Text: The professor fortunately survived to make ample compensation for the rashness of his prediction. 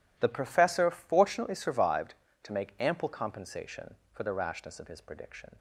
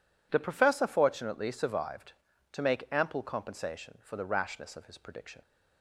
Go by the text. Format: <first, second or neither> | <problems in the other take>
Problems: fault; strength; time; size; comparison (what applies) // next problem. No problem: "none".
neither | none